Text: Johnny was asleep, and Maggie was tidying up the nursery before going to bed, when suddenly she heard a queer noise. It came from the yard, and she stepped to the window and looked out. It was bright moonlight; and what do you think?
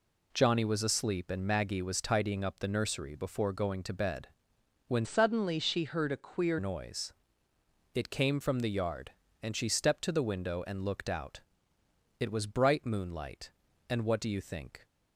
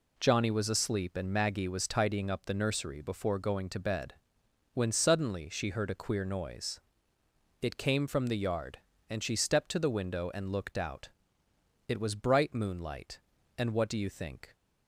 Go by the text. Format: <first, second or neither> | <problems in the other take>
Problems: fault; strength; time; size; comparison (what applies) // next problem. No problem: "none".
second | changes voice from "suddenly" to "queer"; from 5.0 to 6.5 s; 1.5 s long